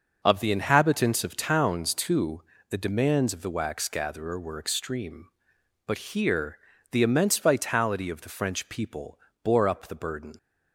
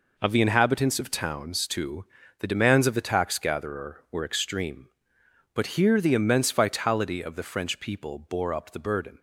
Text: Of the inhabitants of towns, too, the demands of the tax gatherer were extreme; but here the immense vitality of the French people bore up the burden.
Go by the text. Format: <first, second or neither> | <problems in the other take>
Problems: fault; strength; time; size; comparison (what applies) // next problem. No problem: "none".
second | starts louder than the rest; noticeable; until 1.2 s; 6 dB // says "wax" for "tax"; at 3.5 s // pauses between "here" and "the"; slight; at 6.5 s; 0.34 s long // pauses between "people" and "bore"; slight; at 9.1 s; 0.24 s long